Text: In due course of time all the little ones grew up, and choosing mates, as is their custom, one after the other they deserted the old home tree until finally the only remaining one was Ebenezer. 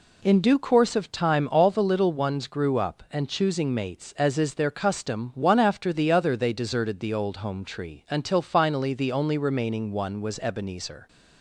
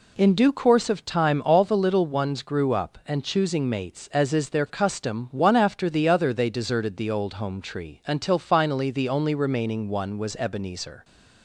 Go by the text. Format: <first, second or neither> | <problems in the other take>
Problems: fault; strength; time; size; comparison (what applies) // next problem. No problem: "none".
neither | none